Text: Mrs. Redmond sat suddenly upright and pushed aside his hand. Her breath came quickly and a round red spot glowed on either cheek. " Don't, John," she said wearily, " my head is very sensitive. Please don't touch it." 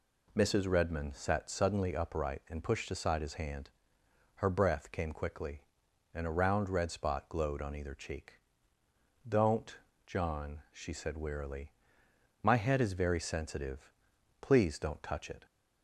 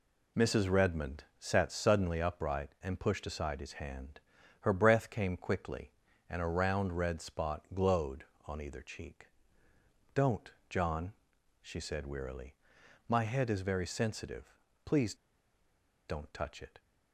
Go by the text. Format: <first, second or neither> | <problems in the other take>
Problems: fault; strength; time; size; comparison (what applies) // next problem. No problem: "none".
first | pauses between "Redmond" and "sat"; slight; at 1.2 s; 0.16 s long // pauses between "Please" and "don't"; noticeable; at 15.1 s; 0.92 s long